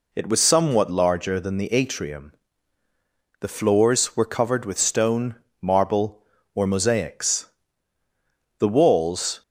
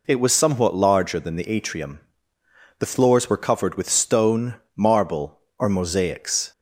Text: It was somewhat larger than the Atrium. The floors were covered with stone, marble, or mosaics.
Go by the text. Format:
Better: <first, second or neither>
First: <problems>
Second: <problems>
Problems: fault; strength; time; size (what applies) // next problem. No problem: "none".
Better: second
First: goes on to say "The walls"; noticeable; from 8.5 s on; 0.84 s long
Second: none